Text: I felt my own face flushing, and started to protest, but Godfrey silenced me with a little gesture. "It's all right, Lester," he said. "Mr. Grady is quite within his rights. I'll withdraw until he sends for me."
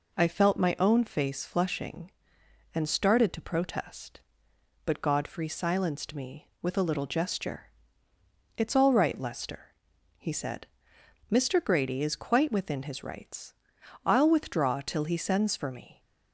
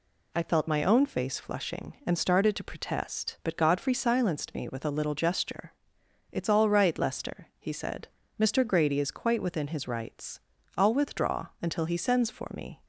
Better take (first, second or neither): second